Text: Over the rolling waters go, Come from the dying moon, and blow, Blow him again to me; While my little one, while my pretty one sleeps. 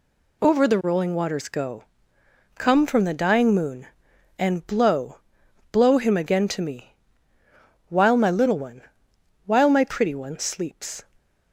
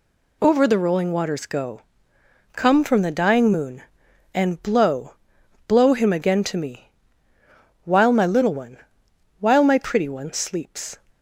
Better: neither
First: none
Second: none

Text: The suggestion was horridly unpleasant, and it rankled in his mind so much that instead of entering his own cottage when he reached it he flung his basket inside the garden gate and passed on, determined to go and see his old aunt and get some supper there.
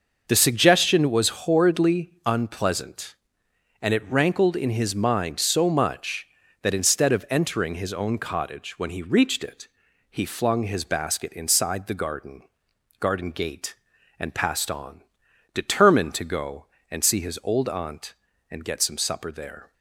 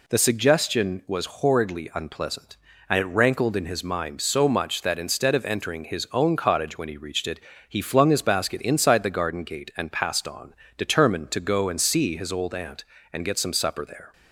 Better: second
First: pauses between "it" and "he"; at 9.6 s; 0.42 s long // says "garden" twice; at 13.0 s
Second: pauses between "it" and "he"; slight; at 7.4 s; 0.28 s long

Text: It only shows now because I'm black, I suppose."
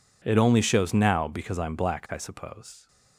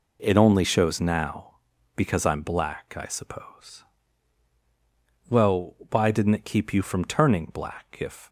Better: first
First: none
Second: goes on to say "Well why didn't it keep you from turning black if"; strong; from 5.2 s on; 2.9 s long

